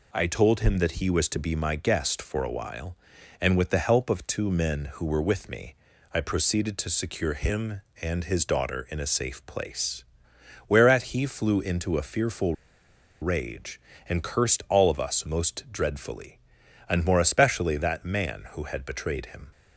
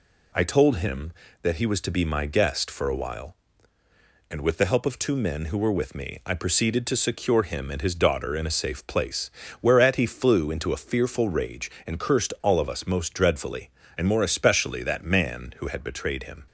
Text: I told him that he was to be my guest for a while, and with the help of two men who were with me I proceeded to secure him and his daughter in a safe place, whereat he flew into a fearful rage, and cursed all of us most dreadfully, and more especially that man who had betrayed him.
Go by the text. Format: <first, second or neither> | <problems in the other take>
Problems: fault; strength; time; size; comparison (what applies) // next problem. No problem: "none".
second | pauses between "me" and "I"; at 5.7 s; 0.38 s long // pauses between "fearful" and "rage"; noticeable; at 12.5 s; 0.66 s long